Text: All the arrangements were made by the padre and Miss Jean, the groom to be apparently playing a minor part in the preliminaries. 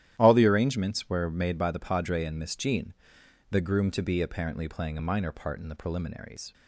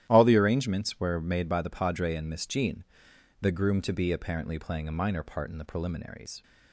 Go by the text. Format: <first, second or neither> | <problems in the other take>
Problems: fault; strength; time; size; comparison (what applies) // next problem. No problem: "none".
neither | starts louder than the rest; strong; the same in both